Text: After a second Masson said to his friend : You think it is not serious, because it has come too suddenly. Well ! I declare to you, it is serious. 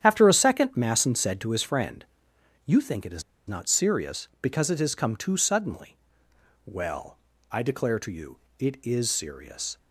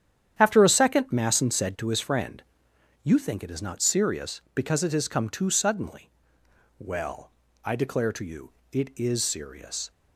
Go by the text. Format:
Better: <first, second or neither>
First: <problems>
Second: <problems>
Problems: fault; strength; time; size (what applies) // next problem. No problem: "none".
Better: second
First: starts louder than the rest; strong; until 1.0 s; 9.5 dB // pauses between "is" and "not"; slight; at 3.2 s; 0.24 s long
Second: starts louder than the rest; strong; until 1.4 s; 9.5 dB